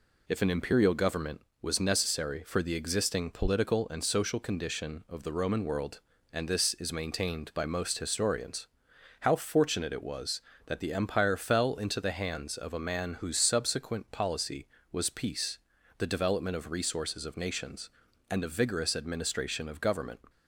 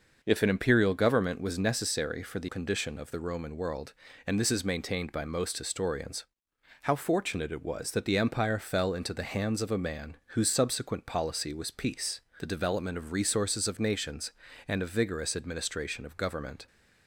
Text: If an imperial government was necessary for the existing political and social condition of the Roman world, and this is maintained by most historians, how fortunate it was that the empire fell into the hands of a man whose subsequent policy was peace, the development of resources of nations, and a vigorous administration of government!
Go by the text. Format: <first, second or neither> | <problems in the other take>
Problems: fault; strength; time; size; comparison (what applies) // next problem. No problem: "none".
first | skips "existing political and social"; at 2.4 s